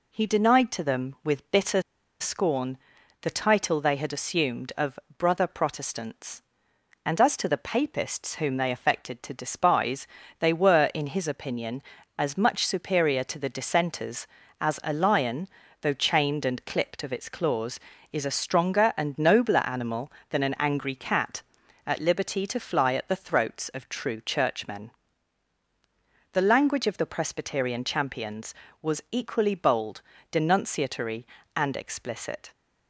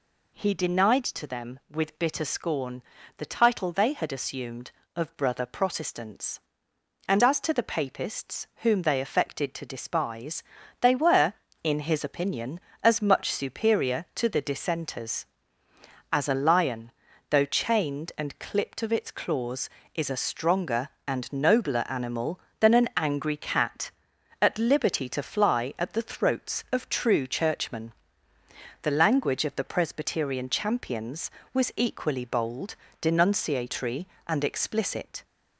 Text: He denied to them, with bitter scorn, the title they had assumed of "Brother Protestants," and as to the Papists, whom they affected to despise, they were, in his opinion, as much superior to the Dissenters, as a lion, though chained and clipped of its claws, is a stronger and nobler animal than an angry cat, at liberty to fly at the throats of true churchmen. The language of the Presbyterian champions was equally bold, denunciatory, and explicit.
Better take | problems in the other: second | pauses between "bitter" and "scorn"; at 1.8 s; 0.39 s long // pauses between "of" and "Brother"; slight; at 4.9 s; 0.22 s long

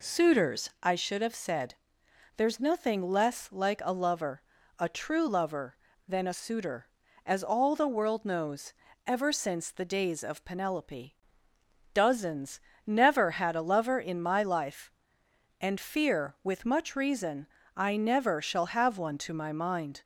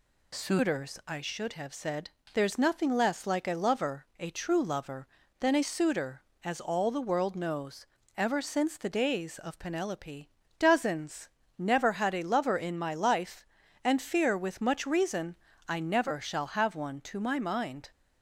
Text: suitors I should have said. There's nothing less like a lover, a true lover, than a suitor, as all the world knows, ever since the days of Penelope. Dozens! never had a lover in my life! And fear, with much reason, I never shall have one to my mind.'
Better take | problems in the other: neither | none

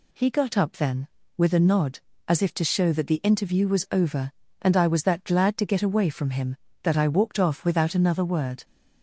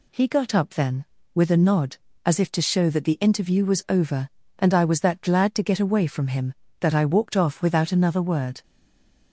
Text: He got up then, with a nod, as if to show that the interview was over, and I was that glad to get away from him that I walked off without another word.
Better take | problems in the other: first | stays silent after the last word; slight; from 8.6 s on; 0.7 s long

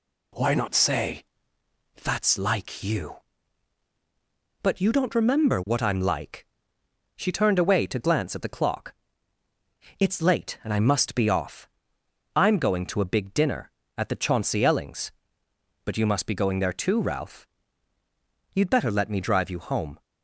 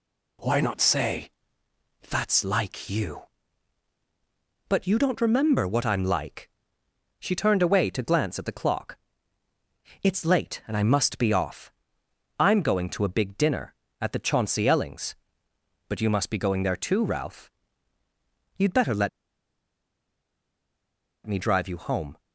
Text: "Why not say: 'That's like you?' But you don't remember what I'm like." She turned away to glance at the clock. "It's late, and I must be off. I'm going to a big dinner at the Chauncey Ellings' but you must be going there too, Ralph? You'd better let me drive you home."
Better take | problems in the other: first | pauses between "let" and "me"; strong; at 19.0 s; 2.1 s long

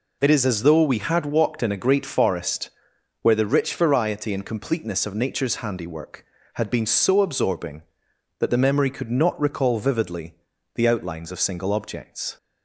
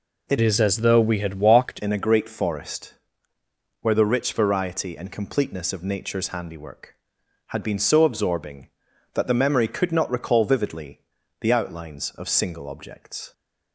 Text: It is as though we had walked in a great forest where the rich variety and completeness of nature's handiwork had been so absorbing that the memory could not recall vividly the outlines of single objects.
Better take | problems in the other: first | changes voice from "is" to "walked"; from 0.3 to 1.8 s; 1.5 s long // pauses between "forest" and "where"; noticeable; at 2.9 s; 0.88 s long; noticeable in the first // pauses between "vividly" and "the"; at 11.0 s; 0.40 s long; also in the first

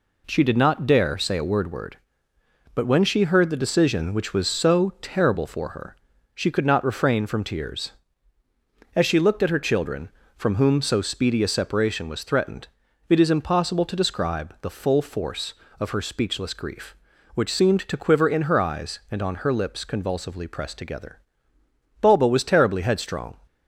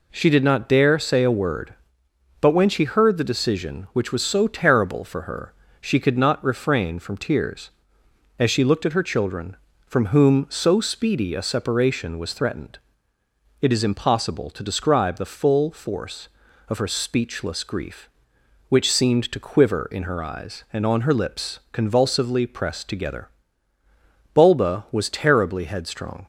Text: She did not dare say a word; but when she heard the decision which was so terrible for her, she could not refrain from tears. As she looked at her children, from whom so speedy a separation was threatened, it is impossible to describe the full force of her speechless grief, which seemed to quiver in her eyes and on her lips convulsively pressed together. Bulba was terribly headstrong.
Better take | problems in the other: second | says "word" twice; at 1.7 s

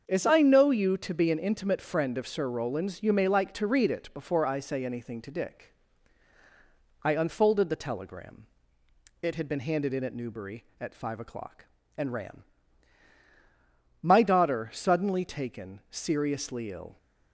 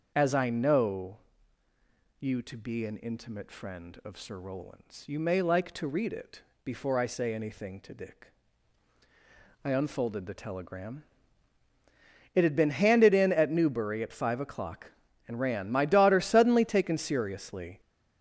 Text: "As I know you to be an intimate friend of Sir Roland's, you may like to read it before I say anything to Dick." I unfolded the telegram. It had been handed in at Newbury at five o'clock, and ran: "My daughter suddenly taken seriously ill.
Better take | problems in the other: first | starts louder than the rest; until 1.1 s; 6.5 dB; also in the first // pauses between "know" and "you"; at 1.1 s; 1.0 s long // pauses between "it" and "before"; slight; at 6.4 s; 0.22 s long // stops before "ill"; at 17.7 s

